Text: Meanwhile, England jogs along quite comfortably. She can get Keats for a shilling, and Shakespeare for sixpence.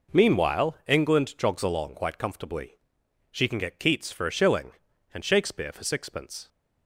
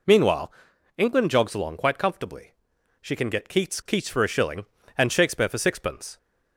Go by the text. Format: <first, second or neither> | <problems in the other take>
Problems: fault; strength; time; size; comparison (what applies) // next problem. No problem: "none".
first | says "Keats" twice; at 3.8 s